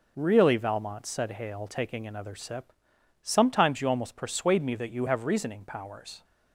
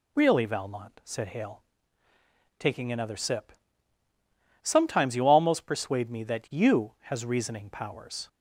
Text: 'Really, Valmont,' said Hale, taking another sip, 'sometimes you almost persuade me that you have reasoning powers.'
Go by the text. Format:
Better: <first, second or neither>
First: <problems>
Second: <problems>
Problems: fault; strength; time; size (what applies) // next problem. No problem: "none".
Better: first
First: none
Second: says "has" for "have"; at 7.0 s